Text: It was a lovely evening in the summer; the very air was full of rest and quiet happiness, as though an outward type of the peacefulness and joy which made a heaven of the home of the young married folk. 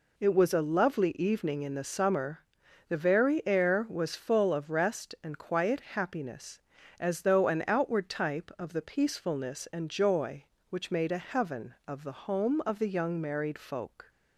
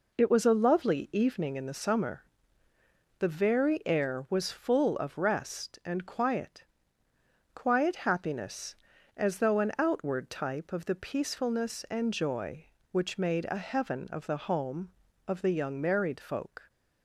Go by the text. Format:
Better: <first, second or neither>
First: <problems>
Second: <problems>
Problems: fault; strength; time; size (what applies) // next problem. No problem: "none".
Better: first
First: none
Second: says "quiet" twice; at 7.5 s